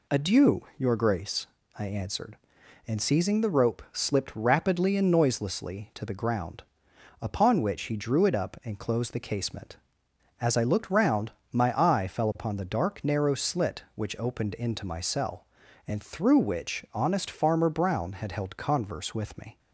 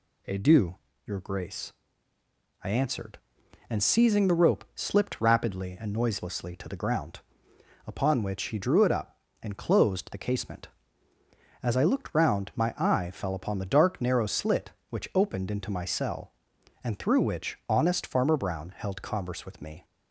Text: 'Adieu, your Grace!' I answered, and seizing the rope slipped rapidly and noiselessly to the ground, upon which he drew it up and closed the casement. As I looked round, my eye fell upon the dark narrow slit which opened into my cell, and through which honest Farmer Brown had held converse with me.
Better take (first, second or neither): first